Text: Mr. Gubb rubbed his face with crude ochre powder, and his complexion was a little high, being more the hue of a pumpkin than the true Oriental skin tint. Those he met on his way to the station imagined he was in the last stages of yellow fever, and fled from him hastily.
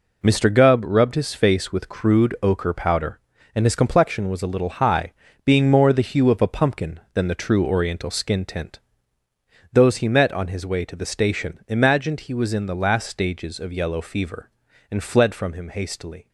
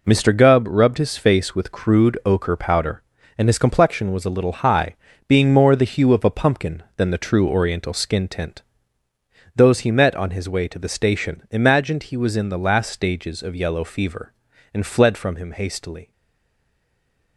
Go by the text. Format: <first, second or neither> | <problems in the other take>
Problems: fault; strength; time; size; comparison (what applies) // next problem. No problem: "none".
first | stays silent after the last word; noticeable; from 16.1 s on; 1.2 s long